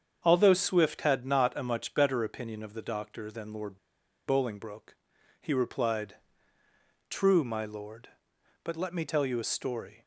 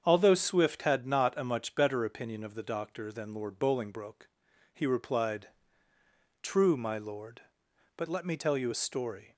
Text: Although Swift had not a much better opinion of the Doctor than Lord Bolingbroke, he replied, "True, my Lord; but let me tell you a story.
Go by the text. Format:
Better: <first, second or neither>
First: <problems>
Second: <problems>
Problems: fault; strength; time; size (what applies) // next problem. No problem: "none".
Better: second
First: starts louder than the rest; strong; until 1.2 s; 7.5 dB // pauses between "Lord" and "Bolingbroke"; noticeable; at 3.7 s; 0.48 s long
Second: starts louder than the rest; strong; until 1.0 s; 7.5 dB